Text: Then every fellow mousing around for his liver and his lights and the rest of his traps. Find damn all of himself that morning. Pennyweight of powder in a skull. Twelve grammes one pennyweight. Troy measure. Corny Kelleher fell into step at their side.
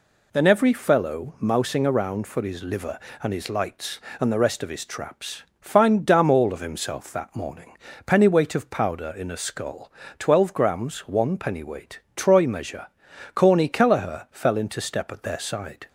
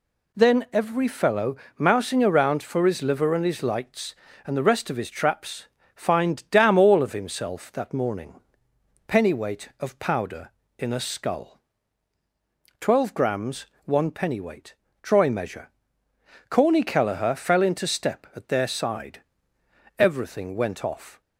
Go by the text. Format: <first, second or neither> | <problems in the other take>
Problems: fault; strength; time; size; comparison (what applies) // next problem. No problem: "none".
first | pauses between "fellow" and "mousing"; slight; at 1.5 s; 0.20 s long // pauses between "grammes" and "one"; slight; at 13.6 s; 0.18 s long // goes on to say "Everything went off"; noticeable; from 19.9 s on; 1.2 s long